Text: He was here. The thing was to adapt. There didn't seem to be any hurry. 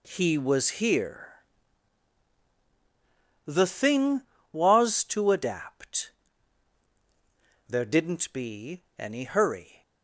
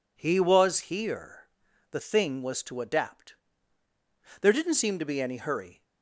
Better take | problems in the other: second | skips "seem to"; at 8.3 s // pauses between "be" and "any"; slight; at 8.8 s; 0.18 s long

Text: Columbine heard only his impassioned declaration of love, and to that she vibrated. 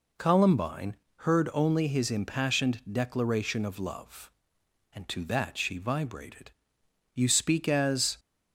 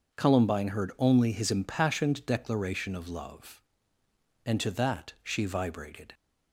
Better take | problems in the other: second | pauses between "Columbine" and "heard"; slight; at 0.9 s; 0.24 s long // goes on to say "You speak as"; noticeable; from 7.1 s on; 1.0 s long

